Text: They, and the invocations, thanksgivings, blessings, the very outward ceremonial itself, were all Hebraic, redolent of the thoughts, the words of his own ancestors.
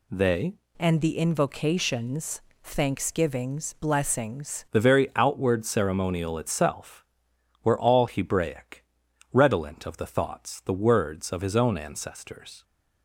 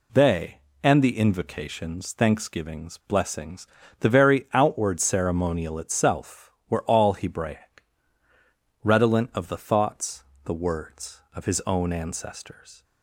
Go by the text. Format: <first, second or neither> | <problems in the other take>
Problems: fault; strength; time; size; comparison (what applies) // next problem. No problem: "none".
second | changes voice from "and" to "blessings"; from 0.7 to 4.6 s; 3.9 s long